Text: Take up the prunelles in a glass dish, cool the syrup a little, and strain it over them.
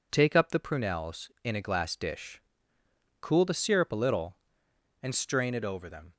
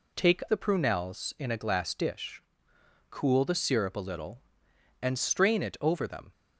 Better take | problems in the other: first | skips "up"; at 0.4 s

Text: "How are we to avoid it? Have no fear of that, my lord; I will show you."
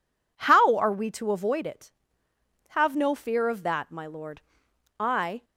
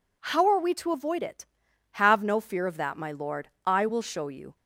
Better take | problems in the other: second | stops before "will show you"; at 5.4 s

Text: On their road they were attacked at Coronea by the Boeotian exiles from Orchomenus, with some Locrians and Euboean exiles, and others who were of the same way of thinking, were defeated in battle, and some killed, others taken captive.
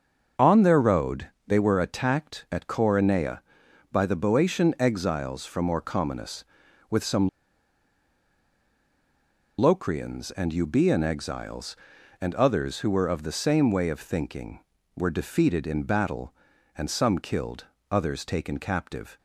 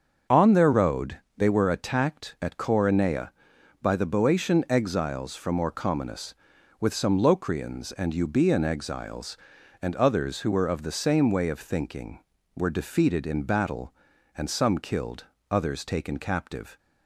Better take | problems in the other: second | starts louder than the rest; until 1.5 s; 7 dB; also in the second // pauses between "road" and "they"; slight; at 1.2 s; 0.18 s long; slight in the second // pauses between "some" and "Locrians"; strong; at 7.2 s; 2.2 s long

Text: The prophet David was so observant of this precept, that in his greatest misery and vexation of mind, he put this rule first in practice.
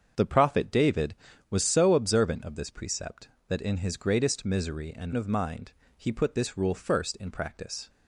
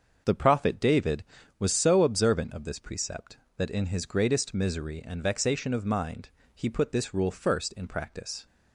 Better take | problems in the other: second | starts louder than the rest; strong; until 1.5 s; 7 dB; also in the second // skips "vexation"; at 5.1 s

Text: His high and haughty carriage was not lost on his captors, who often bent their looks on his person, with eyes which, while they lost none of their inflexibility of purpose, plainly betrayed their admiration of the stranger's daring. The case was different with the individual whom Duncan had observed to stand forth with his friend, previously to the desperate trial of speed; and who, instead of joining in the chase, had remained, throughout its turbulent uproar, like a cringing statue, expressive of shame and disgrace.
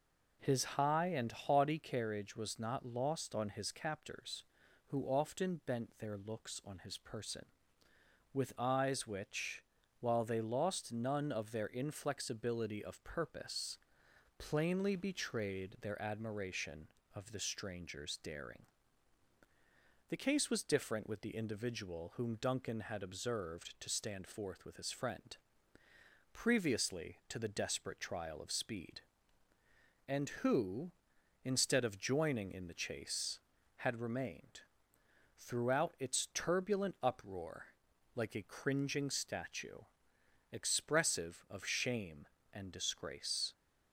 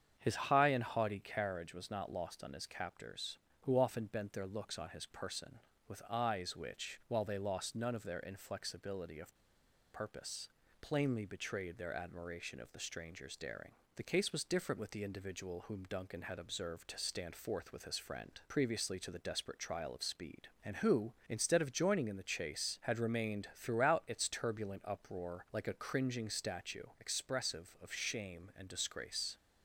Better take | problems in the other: first | starts louder than the rest; strong; until 1.2 s; 8 dB // pauses between "of" and "purpose"; noticeable; at 9.3 s; 0.58 s long

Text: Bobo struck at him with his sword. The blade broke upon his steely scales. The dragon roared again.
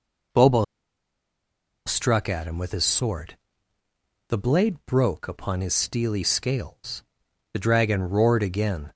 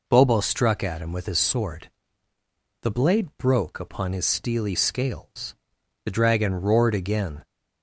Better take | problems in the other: second | pauses between "Bobo" and "struck"; at 0.6 s; 1.2 s long

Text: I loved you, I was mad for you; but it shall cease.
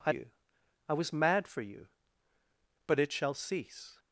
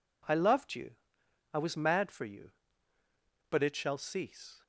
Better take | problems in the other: second | skips "loved"; at 0.1 s

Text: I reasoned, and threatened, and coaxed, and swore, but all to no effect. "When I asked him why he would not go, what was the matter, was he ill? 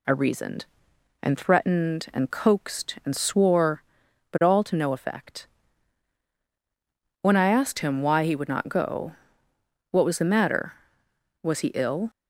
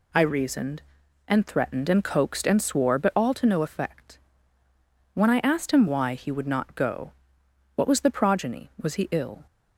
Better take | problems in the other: first | says "progeny" for "matter"; at 8.0 s

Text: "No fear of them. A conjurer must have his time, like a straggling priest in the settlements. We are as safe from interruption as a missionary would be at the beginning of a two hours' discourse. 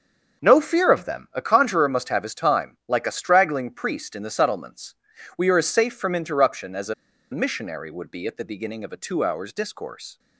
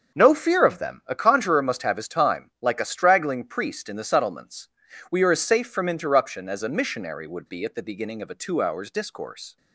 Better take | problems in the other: second | starts louder than the rest; until 1.4 s; 6.5 dB; also in the second // pauses between "a" and "missionary"; at 6.9 s; 0.38 s long

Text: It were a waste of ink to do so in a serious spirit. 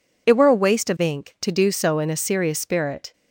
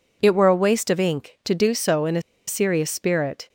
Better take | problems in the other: first | pauses between "a" and "serious"; slight; at 2.2 s; 0.26 s long

